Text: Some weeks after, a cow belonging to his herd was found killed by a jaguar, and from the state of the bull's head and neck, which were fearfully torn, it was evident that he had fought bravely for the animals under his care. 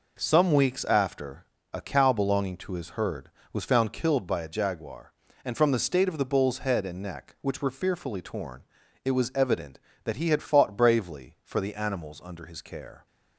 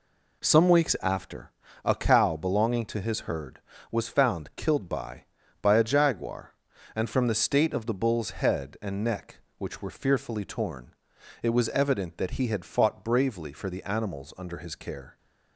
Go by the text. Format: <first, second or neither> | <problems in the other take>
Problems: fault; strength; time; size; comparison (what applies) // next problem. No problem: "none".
first | says "by" twice; at 5.6 s